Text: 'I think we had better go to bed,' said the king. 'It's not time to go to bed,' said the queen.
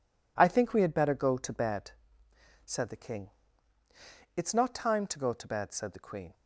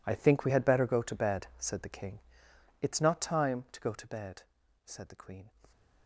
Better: first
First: none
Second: gets quieter; strong; throughout; 17 dB

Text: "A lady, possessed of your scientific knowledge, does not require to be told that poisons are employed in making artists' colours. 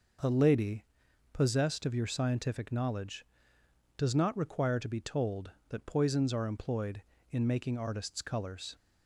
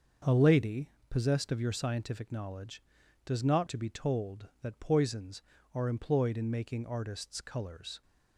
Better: first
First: none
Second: starts louder than the rest; until 1.4 s; 6.5 dB // skips "require"; at 3.6 s

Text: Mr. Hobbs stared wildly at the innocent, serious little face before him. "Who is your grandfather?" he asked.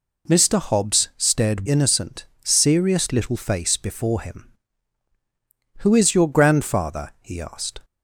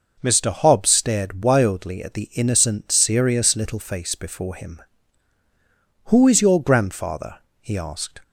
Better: second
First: skips "wildly at the"; at 1.6 s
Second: none

